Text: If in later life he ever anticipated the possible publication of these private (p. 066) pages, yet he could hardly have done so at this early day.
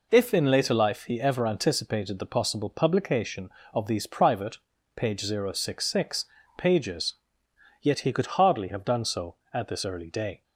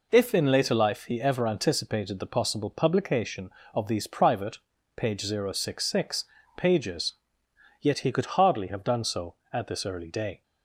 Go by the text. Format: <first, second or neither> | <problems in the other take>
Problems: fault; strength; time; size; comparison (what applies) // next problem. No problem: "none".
neither | none